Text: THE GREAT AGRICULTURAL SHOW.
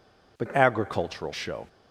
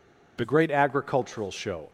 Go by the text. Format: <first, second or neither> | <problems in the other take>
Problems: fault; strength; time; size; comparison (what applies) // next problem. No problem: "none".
second | skips "GREAT"; at 0.5 s